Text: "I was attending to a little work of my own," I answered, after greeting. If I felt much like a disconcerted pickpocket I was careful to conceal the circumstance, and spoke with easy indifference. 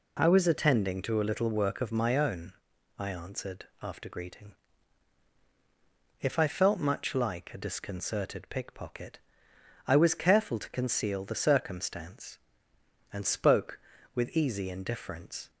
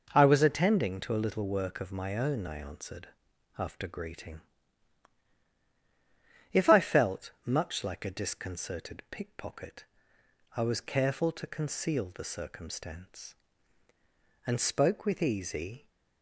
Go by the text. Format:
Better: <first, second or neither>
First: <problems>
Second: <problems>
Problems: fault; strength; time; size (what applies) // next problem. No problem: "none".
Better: first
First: pauses between "pickpocket" and "I"; noticeable; at 9.1 s; 0.68 s long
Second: pauses between "pickpocket" and "I"; noticeable; at 9.8 s; 0.72 s long // stops before "indifference"; at 15.8 s